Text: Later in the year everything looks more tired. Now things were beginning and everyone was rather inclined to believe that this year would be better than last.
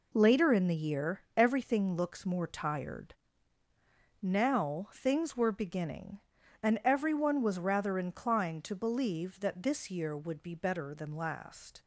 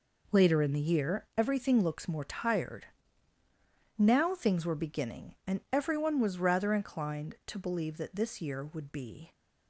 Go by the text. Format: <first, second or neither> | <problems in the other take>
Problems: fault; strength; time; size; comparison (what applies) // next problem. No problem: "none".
first | stops before "better than last"; at 9.3 s